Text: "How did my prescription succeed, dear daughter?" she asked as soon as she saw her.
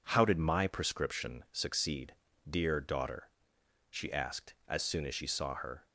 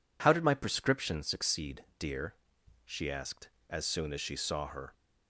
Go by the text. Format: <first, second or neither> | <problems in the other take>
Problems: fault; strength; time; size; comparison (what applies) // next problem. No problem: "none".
first | skips "daughter"; at 2.5 s